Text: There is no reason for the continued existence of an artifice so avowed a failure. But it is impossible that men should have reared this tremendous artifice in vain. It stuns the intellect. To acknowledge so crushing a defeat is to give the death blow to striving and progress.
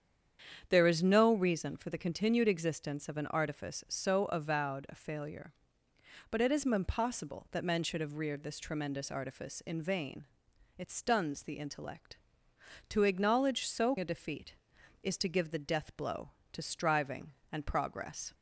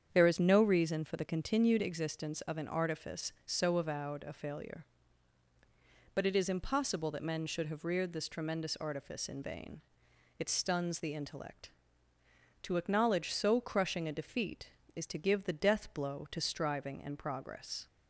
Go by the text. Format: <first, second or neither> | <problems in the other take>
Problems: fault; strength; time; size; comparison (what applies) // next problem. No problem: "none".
second | starts louder than the rest; strong; until 1.6 s; 8 dB; strong in the second // skips "crushing"; at 13.9 s